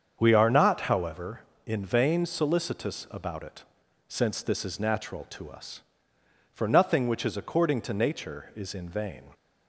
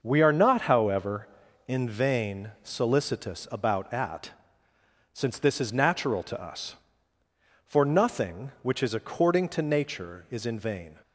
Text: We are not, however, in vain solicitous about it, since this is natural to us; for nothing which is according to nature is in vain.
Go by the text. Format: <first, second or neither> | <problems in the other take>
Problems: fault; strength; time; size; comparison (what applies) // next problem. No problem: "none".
first | starts louder than the rest; until 1.0 s; 6 dB; strong in the first // says "at" for "it"; at 3.9 s